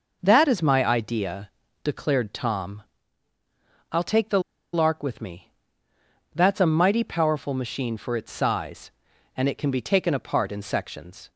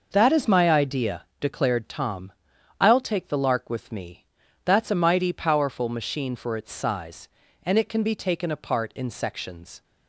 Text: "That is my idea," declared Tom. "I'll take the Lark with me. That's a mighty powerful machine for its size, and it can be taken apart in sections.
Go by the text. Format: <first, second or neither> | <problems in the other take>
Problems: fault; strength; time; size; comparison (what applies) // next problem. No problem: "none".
second | pauses between "the" and "Lark"; slight; at 4.3 s; 0.33 s long